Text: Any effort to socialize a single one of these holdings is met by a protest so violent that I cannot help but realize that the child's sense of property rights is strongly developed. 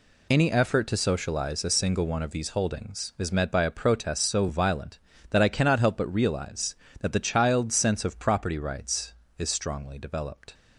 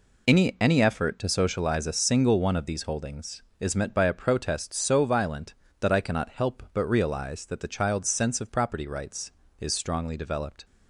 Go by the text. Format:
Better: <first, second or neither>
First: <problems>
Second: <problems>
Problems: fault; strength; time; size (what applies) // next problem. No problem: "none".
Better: first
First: none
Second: says "Any" twice; at 0.6 s